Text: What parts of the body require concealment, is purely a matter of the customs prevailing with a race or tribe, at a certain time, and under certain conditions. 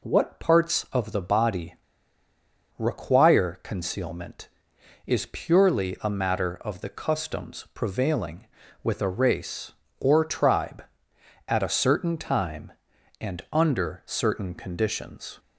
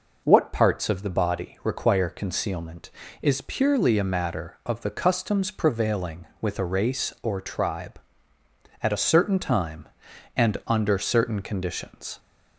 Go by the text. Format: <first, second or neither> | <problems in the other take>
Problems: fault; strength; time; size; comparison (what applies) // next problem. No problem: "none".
second | pauses between "body" and "require"; at 1.7 s; 1.0 s long